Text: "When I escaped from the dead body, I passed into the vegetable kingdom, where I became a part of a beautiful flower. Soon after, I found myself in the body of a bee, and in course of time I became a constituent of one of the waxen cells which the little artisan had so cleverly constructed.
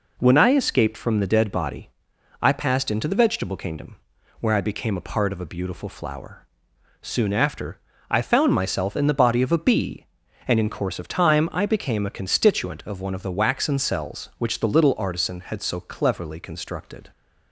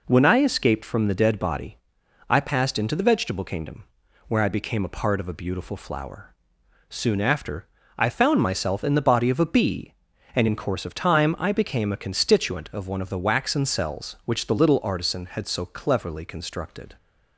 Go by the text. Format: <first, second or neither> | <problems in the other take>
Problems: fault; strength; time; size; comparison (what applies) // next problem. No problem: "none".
neither | none